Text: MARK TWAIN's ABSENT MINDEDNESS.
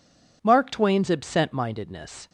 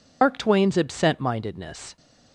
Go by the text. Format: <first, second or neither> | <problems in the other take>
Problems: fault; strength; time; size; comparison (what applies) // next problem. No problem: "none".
first | loses the start of "MARK"; at 0.2 s; 130 ms